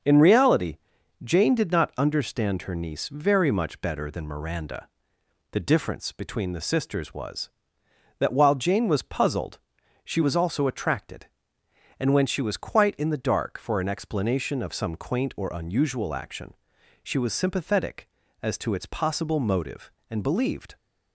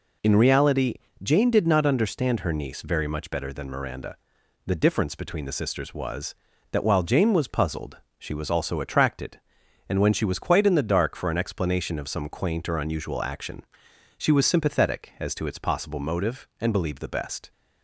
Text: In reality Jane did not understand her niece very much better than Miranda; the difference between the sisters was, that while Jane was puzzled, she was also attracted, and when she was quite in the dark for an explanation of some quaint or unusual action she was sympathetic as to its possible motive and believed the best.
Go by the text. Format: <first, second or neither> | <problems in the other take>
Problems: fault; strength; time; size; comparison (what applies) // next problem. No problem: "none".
second | starts louder than the rest; until 1.5 s; 6.5 dB // pauses between "reality" and "Jane"; noticeable; at 0.7 s; 0.46 s long; slight in the second // pauses between "action" and "she"; noticeable; at 16.5 s; 0.48 s long; noticeable in the second // stops before "the best"; at 20.7 s